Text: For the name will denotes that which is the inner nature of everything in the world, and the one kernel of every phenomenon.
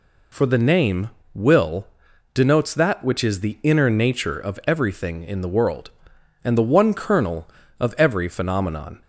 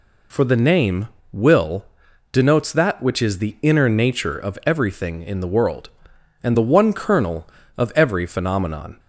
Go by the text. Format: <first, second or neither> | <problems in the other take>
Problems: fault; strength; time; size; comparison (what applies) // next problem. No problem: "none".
neither | pauses between "will" and "denotes"; noticeable; the same in both